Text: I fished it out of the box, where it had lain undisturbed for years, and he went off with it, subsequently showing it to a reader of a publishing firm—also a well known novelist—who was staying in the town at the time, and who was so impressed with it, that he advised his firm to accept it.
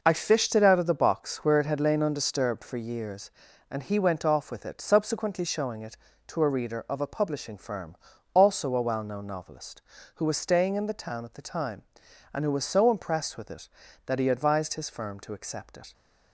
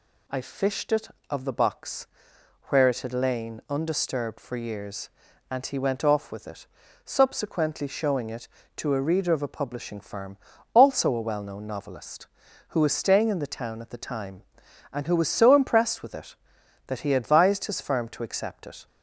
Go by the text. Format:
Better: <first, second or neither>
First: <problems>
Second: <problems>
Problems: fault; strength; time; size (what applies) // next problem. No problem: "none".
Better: first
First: none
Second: skips "out"; at 1.1 s